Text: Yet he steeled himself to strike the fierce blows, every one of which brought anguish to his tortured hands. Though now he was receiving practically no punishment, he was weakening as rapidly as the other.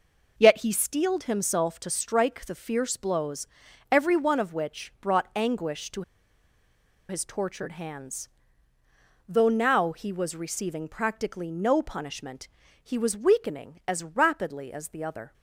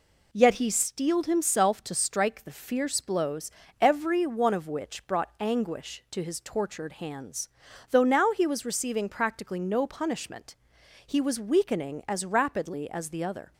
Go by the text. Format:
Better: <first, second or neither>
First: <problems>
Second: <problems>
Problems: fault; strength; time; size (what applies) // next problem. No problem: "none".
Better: second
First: pauses between "to" and "his"; at 6.0 s; 1.0 s long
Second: none